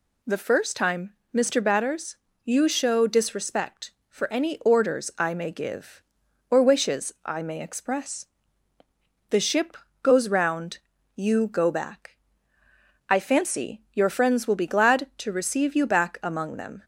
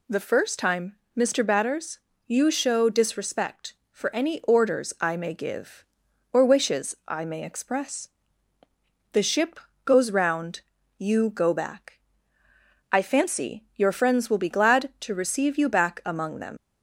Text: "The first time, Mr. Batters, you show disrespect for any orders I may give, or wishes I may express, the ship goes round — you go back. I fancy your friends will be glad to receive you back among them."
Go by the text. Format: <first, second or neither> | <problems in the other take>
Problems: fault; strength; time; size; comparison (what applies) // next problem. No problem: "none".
first | pauses between "ship" and "goes"; slight; at 9.5 s; 0.28 s long; slight in the first // leaves "them" unfinished; at 16.5 s; 95 ms